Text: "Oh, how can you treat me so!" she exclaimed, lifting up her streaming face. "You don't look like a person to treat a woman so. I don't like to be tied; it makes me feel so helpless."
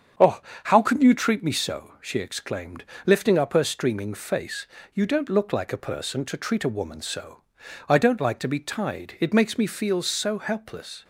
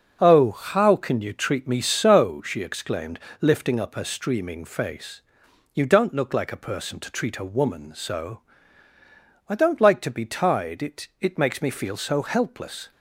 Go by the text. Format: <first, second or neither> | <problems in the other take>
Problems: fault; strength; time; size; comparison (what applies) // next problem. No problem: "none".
first | starts louder than the rest; until 1.2 s; 6 dB; strong in the first // says "it" twice; at 11.1 s